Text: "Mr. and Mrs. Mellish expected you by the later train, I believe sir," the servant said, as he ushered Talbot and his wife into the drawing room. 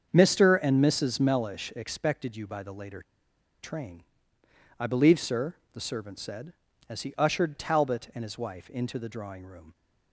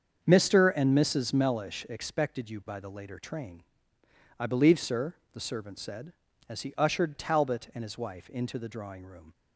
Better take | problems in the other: second | starts louder than the rest; until 1.1 s; 7 dB; also in the second // pauses between "later" and "train"; noticeable; at 3.0 s; 0.60 s long

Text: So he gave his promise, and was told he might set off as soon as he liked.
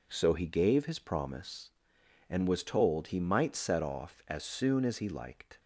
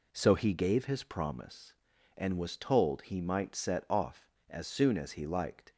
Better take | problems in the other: neither | none

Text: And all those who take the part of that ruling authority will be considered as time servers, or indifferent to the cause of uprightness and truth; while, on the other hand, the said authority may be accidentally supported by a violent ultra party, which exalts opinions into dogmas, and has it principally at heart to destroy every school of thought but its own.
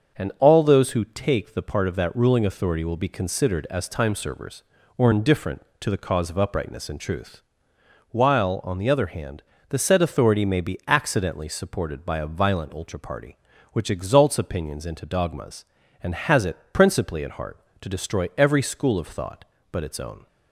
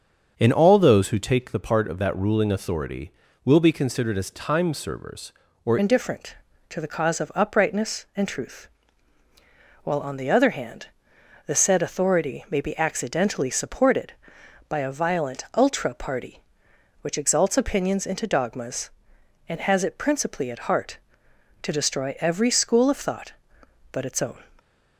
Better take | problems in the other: first | starts louder than the rest; until 1.3 s; 6.5 dB; also in the first // changes voice at "indifferent"; from 5.7 s on; 18.7 s long

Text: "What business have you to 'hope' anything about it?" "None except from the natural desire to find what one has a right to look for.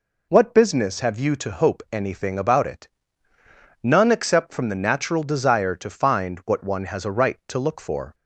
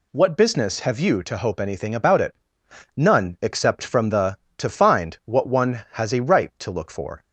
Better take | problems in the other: first | skips "natural desire"; at 4.4 s

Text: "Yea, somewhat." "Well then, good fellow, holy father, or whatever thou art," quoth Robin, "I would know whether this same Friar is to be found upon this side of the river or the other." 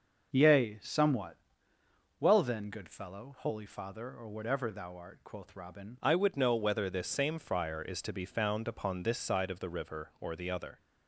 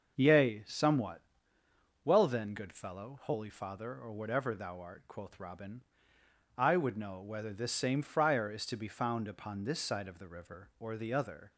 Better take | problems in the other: second | starts louder than the rest; noticeable; until 1.3 s; 6 dB; also in the second // changes voice at "I"; from 5.9 s on; 4.8 s long

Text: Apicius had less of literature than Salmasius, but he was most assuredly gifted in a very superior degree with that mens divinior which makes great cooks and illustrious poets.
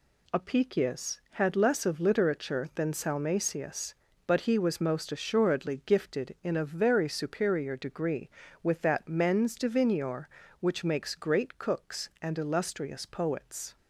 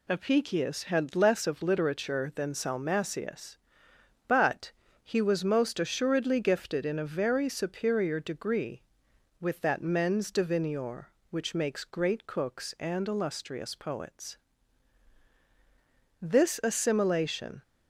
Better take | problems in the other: first | pauses between "but" and "he"; slight; at 4.7 s; 0.32 s long // goes on to say "This assimilation"; from 16.1 s on; 1.4 s long

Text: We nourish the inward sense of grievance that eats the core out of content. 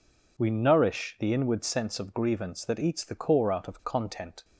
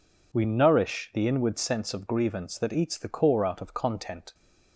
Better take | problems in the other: neither | none

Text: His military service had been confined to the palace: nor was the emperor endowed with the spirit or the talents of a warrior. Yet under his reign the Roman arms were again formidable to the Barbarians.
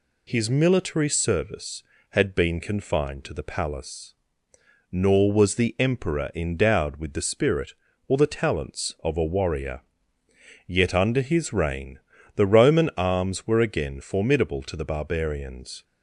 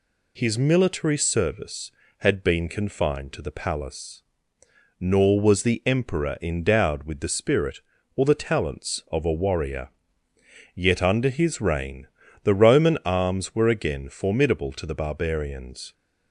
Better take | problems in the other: neither | pauses between "reign" and "the"; slight; the same in both

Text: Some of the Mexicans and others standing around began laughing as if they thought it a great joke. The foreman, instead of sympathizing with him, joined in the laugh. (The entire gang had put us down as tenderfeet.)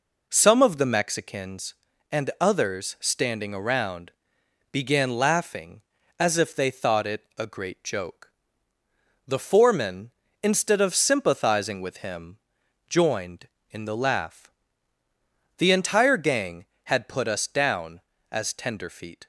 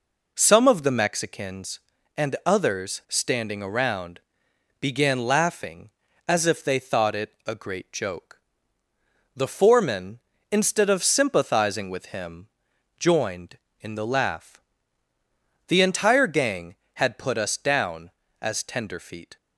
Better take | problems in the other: neither | pauses between "around" and "began"; noticeable; the same in both

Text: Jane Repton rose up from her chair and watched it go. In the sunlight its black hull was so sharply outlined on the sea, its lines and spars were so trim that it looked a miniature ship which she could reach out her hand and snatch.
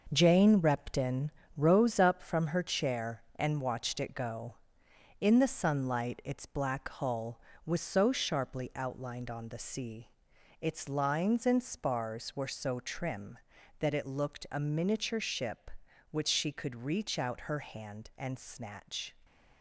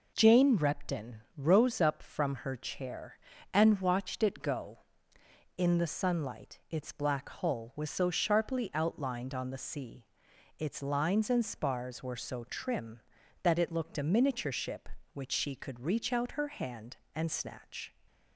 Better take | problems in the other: second | gets quieter; strong; throughout; 7 dB // pauses between "Repton" and "rose"; slight; at 1.3 s; 0.26 s long // stays silent after the last word; slight; from 19.1 s on; 0.5 s long

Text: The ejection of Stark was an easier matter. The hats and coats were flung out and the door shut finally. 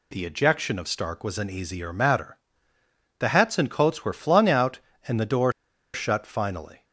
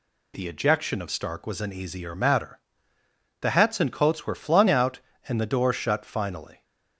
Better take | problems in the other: second | pauses between "door" and "shut"; at 5.5 s; 0.41 s long

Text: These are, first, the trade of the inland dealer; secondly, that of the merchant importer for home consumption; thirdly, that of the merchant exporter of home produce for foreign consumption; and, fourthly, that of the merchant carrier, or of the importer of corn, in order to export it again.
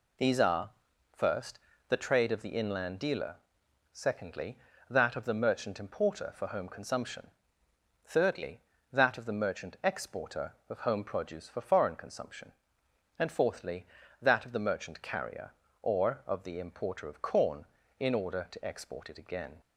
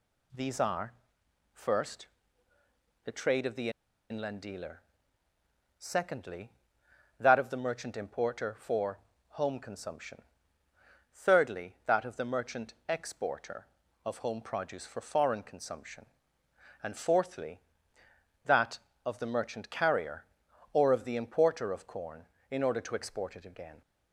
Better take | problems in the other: first | pauses between "the" and "inland"; at 3.6 s; 0.41 s long // pauses between "for" and "home"; slight; at 8.9 s; 0.30 s long

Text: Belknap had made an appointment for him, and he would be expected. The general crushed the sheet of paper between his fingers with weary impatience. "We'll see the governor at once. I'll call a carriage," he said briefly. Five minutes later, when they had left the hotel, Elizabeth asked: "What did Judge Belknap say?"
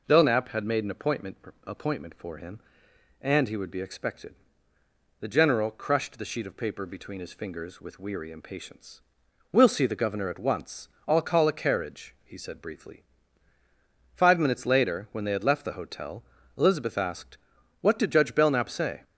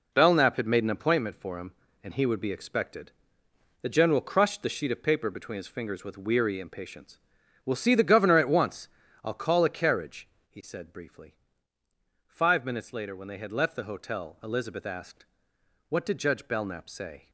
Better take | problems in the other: second | says "appointment" twice; at 1.6 s

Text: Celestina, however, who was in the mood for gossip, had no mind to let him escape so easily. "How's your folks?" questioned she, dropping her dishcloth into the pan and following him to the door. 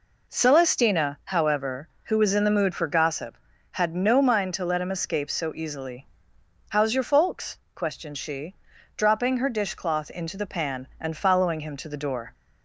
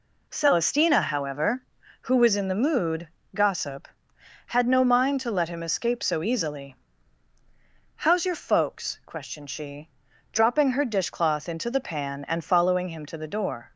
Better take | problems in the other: first | skips "for"; at 3.2 s

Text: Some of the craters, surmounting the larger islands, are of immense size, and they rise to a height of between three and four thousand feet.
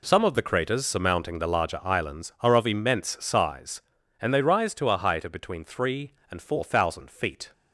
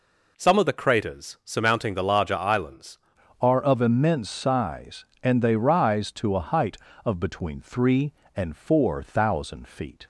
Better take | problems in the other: first | changes voice at "are"; from 3.4 s on; 6.6 s long

